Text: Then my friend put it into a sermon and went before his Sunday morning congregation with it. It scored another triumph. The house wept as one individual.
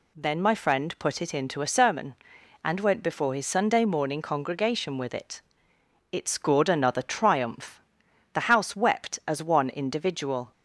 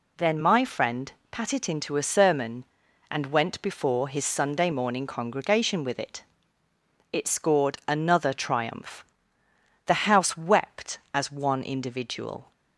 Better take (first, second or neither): first